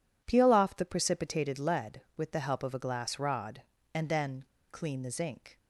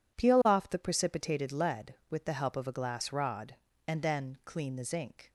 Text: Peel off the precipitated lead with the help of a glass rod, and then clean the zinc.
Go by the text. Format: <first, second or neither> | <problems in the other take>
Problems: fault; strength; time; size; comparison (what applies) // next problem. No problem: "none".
second | pauses between "then" and "clean"; slight; at 4.4 s; 0.25 s long